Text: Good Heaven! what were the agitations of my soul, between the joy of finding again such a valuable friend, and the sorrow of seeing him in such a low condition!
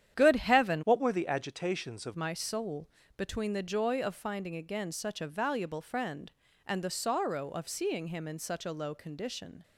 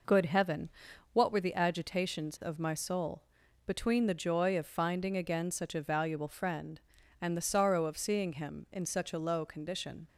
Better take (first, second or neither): second